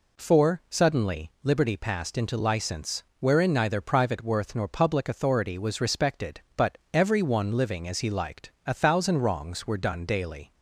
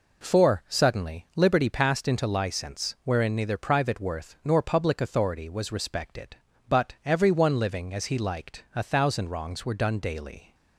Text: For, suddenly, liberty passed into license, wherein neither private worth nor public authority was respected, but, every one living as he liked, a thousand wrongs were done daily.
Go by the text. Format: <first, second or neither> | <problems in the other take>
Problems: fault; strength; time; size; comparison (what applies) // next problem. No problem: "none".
neither | none